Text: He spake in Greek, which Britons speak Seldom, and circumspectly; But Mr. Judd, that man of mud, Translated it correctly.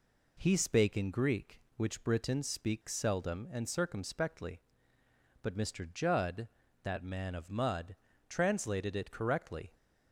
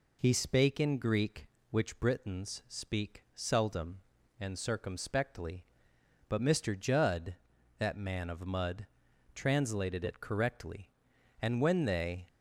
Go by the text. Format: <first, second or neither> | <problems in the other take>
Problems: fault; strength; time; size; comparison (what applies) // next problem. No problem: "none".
first | goes on to say "And when they"; noticeable; from 11.4 s on; 0.86 s long